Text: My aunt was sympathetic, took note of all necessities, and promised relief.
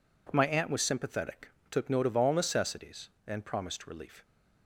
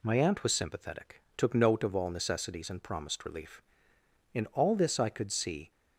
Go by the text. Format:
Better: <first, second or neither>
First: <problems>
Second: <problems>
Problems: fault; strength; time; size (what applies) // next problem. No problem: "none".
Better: first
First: none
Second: goes on to say "In all this I could see"; from 4.3 s on; 1.3 s long